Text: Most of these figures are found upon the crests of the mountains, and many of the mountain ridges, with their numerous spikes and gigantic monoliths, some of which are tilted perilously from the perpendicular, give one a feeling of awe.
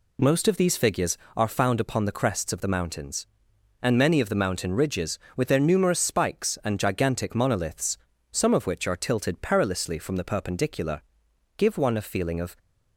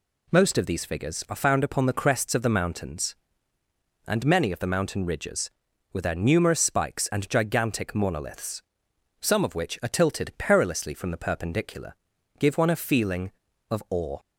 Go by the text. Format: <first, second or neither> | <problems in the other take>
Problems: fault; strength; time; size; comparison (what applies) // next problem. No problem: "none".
second | stops before "awe"; at 12.5 s